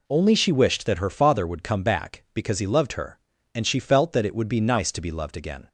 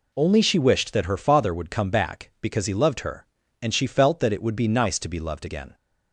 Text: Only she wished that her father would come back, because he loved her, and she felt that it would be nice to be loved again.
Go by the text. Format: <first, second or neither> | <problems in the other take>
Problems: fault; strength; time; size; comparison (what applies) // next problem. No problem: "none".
neither | none